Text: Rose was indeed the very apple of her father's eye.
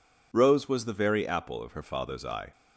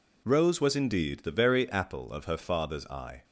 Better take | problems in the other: second | skips "indeed"; at 0.8 s

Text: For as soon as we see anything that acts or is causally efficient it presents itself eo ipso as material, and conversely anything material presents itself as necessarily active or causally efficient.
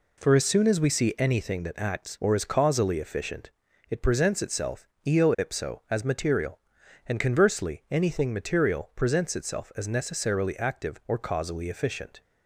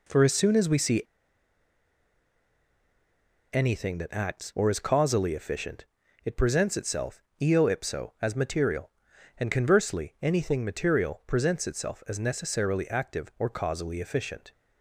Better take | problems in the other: first | pauses between "see" and "anything"; strong; at 1.0 s; 2.4 s long // pauses between "efficient" and "it"; at 5.8 s; 0.38 s long; also in the first // pauses between "itself" and "eo"; slight; at 7.1 s; 0.22 s long; slight in the first

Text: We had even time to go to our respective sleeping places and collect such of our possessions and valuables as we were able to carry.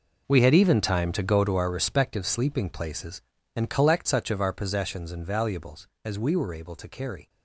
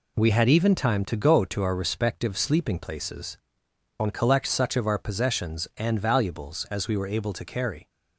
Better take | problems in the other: second | gets quieter; strong; throughout; 13.5 dB

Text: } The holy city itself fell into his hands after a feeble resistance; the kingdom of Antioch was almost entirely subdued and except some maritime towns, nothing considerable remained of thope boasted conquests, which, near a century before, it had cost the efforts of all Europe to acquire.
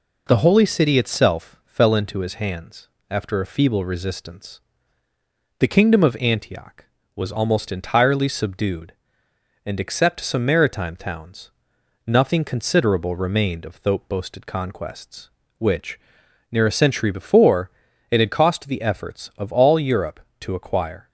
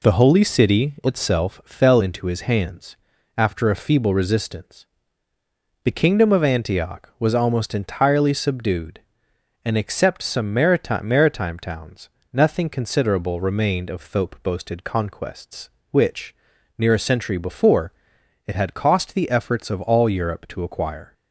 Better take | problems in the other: first | pauses between "hands" and "after"; at 2.9 s; 0.42 s long; slight in the first // says "maritime" twice; at 11.0 s

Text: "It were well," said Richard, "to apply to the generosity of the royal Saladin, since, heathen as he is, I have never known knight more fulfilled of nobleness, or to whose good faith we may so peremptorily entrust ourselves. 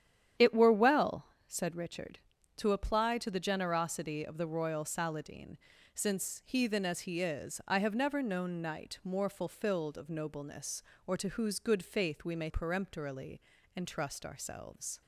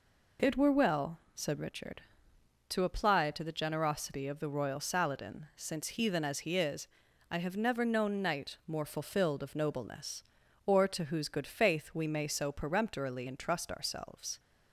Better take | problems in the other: second | starts louder than the rest; strong; until 1.6 s; 9.5 dB // skips "so"; at 12.5 s // pauses between "peremptorily" and "entrust"; slight; at 13.4 s; 0.34 s long

